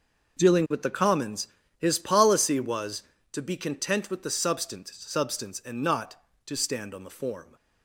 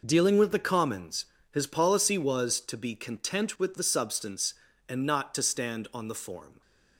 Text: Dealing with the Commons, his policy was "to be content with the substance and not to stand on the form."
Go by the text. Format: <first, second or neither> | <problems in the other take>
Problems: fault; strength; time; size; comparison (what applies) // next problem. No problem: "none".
second | says "substance" twice; at 4.9 s